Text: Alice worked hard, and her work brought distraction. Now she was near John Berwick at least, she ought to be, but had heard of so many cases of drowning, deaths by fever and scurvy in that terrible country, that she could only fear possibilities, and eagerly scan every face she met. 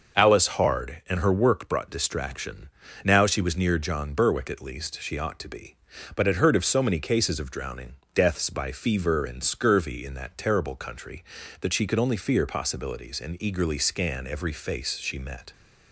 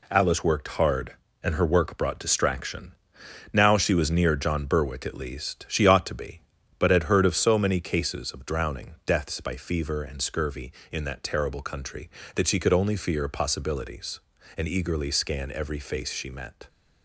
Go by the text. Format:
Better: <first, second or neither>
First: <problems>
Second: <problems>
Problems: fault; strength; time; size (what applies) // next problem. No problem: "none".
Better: second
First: skips "worked"; at 0.4 s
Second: none